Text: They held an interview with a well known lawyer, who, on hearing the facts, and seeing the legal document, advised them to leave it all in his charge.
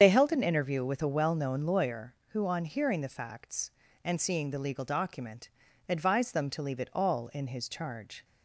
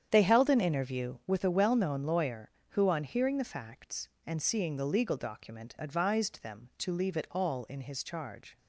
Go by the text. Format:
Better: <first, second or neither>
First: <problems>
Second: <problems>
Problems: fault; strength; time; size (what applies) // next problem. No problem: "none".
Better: second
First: loses the start of "They"; at 0.0 s; 45 ms // starts louder than the rest; strong; until 1.0 s; 8 dB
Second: starts louder than the rest; strong; until 1.1 s; 8.5 dB